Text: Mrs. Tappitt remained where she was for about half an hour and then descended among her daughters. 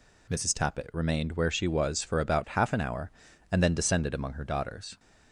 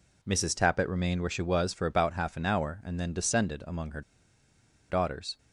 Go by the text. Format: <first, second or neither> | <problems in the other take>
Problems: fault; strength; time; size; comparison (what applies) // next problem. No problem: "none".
first | pauses between "her" and "daughters"; noticeable; at 4.0 s; 0.88 s long